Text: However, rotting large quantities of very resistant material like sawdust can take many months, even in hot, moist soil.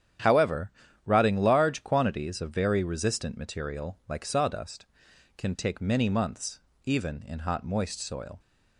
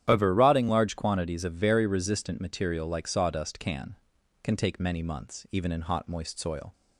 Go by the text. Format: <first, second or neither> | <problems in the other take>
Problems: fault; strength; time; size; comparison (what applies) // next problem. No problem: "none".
first | starts louder than the rest; strong; until 1.0 s; 10.5 dB; strong in the first // says "can" twice; at 4.4 s